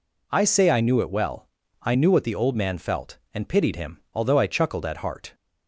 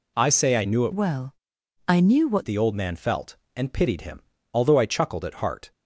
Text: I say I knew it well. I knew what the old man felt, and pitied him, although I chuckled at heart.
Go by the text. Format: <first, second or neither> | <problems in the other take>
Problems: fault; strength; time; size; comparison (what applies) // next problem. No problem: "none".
first | changes voice from "well" to "what"; from 0.9 to 2.4 s; 1.5 s long